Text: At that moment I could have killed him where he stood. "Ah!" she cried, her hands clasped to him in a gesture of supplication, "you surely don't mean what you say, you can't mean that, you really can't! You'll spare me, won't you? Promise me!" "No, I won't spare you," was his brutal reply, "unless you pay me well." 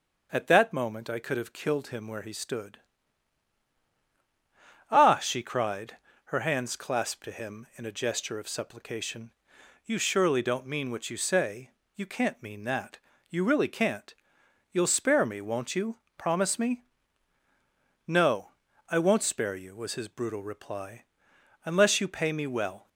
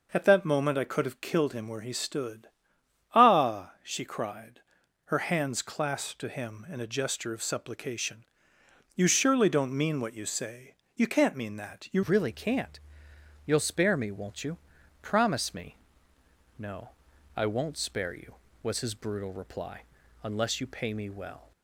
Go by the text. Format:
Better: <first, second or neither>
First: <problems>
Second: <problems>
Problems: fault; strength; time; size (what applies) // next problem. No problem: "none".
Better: first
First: none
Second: changes voice at "really"; from 12.0 s on; 9.5 s long